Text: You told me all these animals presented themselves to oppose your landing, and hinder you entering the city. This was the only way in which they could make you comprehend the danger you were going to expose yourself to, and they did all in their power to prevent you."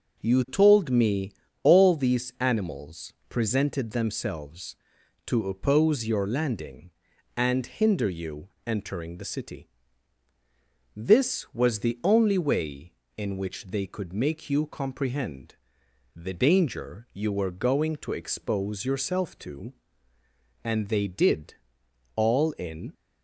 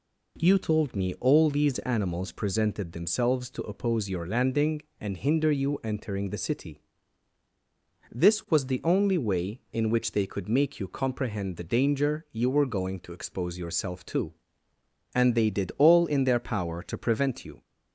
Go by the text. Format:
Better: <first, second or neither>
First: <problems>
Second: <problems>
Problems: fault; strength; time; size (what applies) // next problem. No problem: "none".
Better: second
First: pauses between "me" and "all"; slight; at 1.3 s; 0.32 s long // pauses between "animals" and "presented"; slight; at 3.1 s; 0.16 s long // pauses between "you" and "entering"; slight; at 8.4 s; 0.18 s long // pauses between "comprehend" and "the"; noticeable; at 15.5 s; 0.58 s long // pauses between "did" and "all"; noticeable; at 21.5 s; 0.60 s long // stops before "their power to prevent you"; at 22.9 s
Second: none